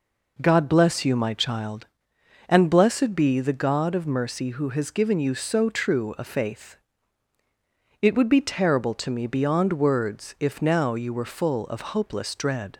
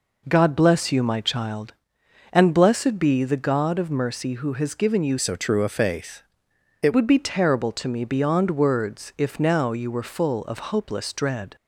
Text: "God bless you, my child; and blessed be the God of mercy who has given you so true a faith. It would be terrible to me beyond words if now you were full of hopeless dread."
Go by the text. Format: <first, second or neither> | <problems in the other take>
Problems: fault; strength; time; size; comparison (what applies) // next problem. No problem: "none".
first | changes voice from "so" to "It"; from 5.1 to 6.9 s; 1.8 s long